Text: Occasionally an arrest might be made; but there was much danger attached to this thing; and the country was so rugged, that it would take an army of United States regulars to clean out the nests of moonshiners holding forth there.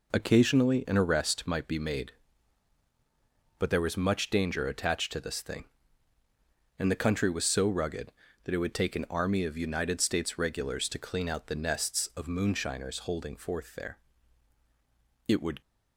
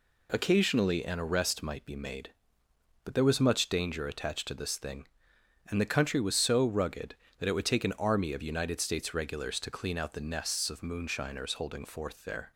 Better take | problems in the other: second | goes on to say "It would"; slight; from 15.2 s on; 0.34 s long

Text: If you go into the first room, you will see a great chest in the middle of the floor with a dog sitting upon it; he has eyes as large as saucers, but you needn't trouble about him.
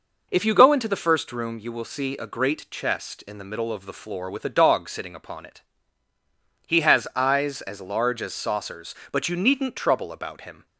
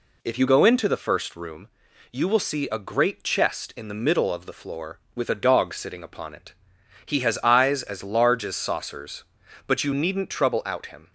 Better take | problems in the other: first | says "out" for "about"; at 10.6 s

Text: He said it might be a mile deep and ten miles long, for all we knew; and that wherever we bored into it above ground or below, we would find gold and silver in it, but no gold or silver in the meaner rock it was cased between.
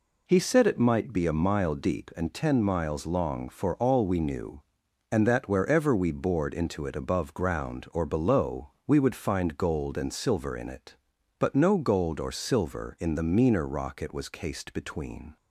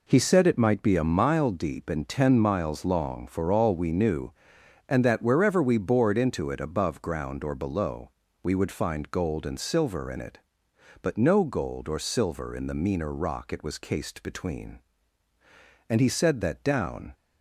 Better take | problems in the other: first | goes on to say "And he said that down"; noticeable; from 15.8 s on; 1.2 s long

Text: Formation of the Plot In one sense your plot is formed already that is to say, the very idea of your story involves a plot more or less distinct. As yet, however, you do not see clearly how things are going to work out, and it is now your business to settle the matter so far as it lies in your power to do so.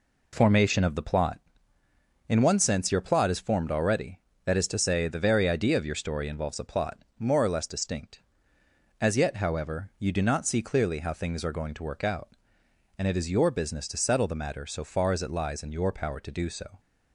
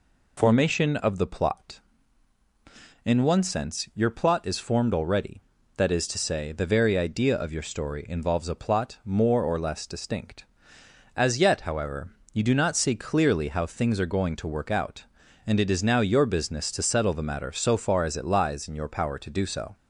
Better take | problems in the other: second | pauses between "plot" and "more"; slight; at 6.9 s; 0.22 s long // skips "now"; at 13.2 s

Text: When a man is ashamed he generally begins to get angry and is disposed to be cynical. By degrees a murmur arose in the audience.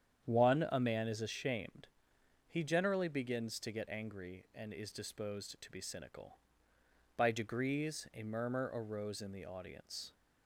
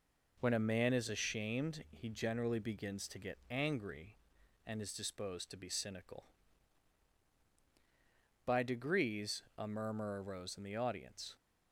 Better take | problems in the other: second | starts louder than the rest; strong; until 1.2 s; 8.5 dB // says "One" for "When"; at 0.2 s // pauses between "ashamed" and "he"; noticeable; at 1.8 s; 0.60 s long

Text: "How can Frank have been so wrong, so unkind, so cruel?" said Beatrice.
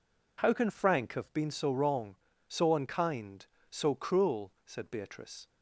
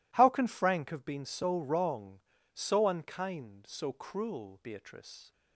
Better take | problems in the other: first | skips "said"; at 4.6 s

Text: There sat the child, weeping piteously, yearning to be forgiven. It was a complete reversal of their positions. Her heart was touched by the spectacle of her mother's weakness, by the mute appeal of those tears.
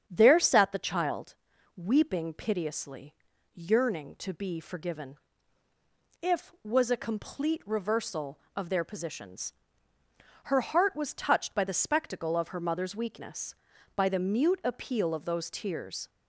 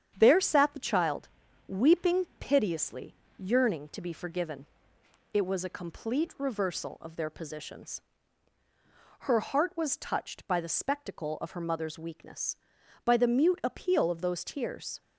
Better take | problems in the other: second | starts louder than the rest; strong; until 1.0 s; 8.5 dB; strong in the second // says "If" for "It"; at 6.2 s

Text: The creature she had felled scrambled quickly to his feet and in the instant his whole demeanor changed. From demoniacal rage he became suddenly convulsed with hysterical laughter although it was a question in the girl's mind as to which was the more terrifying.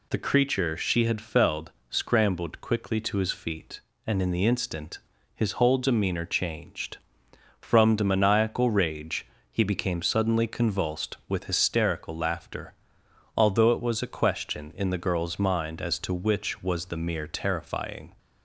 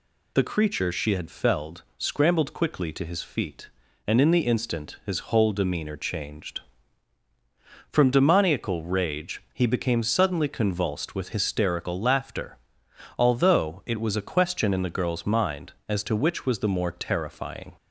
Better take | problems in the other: second | pauses between "felled" and "scrambled"; slight; at 1.7 s; 0.18 s long // pauses between "instant" and "his"; slight; at 4.9 s; 0.36 s long // pauses between "rage" and "he"; slight; at 9.2 s; 0.26 s long // pauses between "laughter" and "although"; noticeable; at 12.7 s; 0.62 s long; noticeable in the second // says "mere" for "more"; at 16.9 s

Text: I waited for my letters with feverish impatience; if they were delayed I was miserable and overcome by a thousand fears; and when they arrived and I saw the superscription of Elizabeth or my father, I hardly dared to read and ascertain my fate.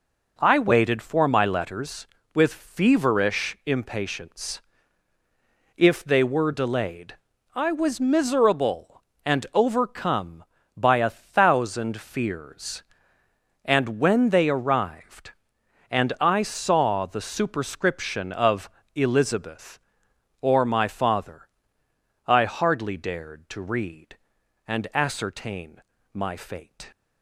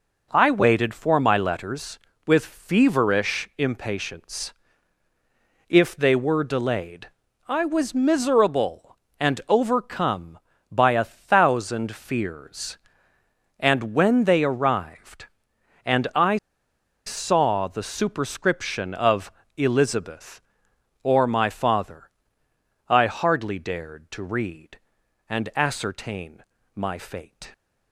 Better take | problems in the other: first | pauses between "delayed" and "I"; at 7.0 s; 0.40 s long; also in the first // pauses between "I" and "saw"; noticeable; at 16.3 s; 0.69 s long // pauses between "of" and "Elizabeth"; slight; at 19.3 s; 0.24 s long; slight in the first // pauses between "ascertain" and "my"; slight; at 26.4 s; 0.32 s long; slight in the first

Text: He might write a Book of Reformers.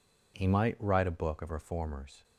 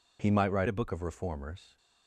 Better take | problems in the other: first | changes voice from "a" to "Book"; from 0.6 to 0.8 s; 0.2 s long

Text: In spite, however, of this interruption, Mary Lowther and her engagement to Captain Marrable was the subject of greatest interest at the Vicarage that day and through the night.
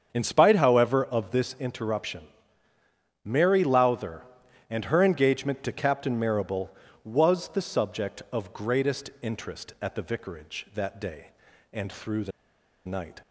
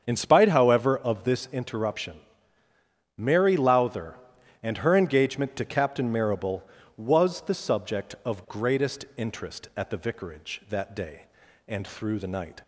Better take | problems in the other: second | starts louder than the rest; strong; until 1.1 s; 7 dB; strong in the second // pauses between "the" and "night"; noticeable; at 12.3 s; 0.55 s long

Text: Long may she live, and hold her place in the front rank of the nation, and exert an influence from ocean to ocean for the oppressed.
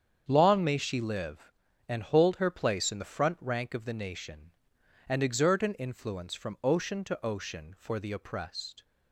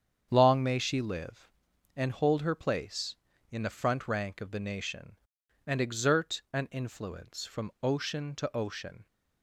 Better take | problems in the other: first | starts louder than the rest; strong; until 1.3 s; 8 dB; strong in the first // stops before "for the oppressed"; at 9.0 s

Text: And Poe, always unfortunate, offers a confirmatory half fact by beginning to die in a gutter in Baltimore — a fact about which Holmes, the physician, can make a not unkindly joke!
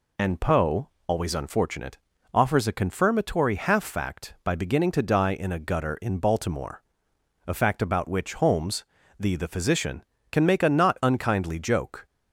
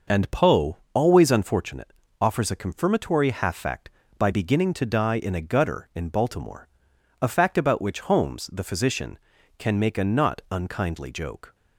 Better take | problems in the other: second | says "the" twice; at 9.3 s

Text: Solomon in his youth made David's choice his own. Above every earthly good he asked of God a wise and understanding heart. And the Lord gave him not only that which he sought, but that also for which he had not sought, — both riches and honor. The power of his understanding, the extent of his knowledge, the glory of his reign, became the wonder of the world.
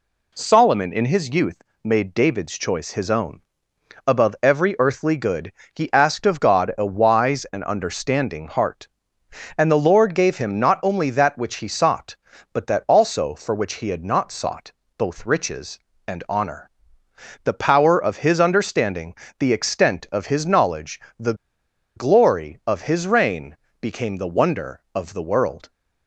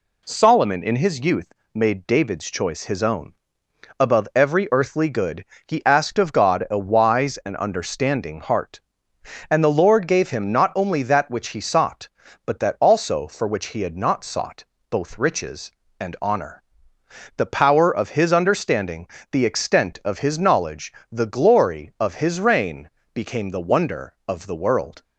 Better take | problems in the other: second | pauses between "youth" and "made"; slight; at 1.6 s; 0.22 s long; slight in the second // pauses between "good" and "he"; slight; at 5.5 s; 0.24 s long; slight in the second // pauses between "the" and "glory"; noticeable; at 21.3 s; 0.61 s long

